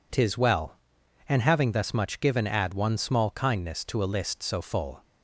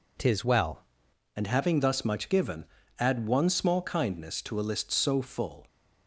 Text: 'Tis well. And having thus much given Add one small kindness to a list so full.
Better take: first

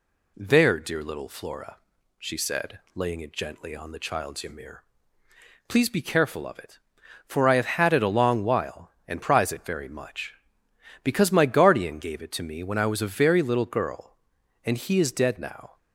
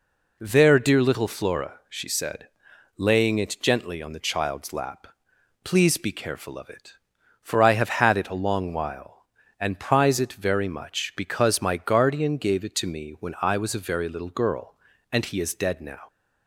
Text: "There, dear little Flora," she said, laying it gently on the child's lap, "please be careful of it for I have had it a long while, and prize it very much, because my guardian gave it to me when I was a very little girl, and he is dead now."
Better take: second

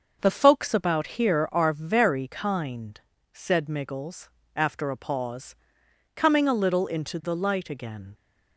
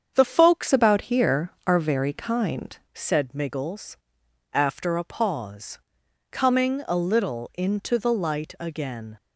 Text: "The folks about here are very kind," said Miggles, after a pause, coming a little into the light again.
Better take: first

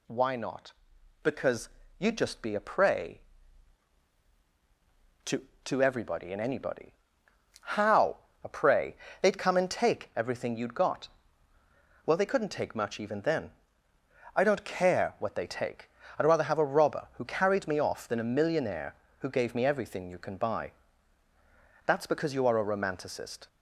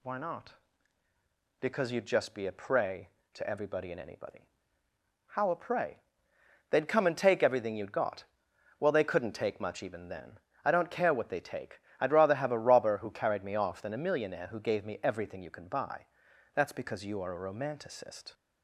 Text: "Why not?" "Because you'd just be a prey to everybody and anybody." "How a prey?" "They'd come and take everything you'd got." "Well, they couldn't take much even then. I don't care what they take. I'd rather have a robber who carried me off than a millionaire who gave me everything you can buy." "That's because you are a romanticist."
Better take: second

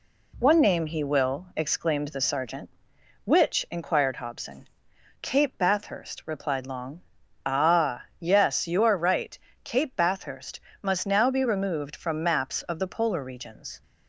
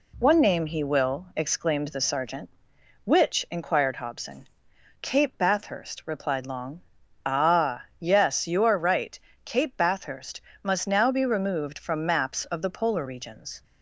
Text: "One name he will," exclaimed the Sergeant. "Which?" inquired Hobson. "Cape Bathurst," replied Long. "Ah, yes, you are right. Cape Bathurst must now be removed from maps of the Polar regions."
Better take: neither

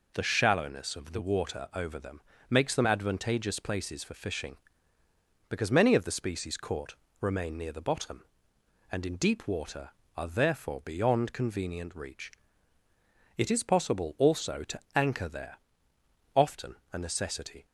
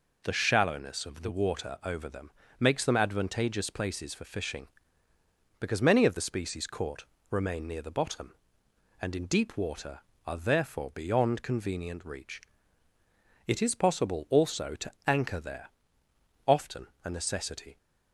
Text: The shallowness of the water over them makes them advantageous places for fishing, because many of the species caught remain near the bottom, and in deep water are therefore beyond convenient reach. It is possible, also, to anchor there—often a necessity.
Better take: neither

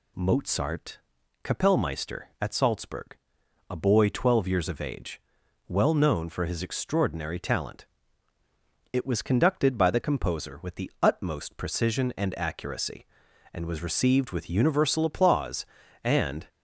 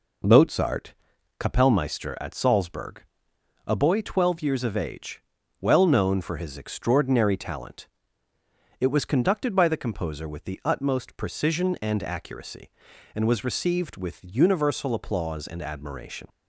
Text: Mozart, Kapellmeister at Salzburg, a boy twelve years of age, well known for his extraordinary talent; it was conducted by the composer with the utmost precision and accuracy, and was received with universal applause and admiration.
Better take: second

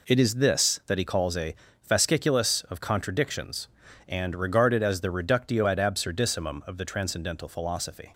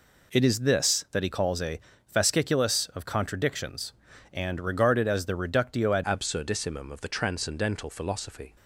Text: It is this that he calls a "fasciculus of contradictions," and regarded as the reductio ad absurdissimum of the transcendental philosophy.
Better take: first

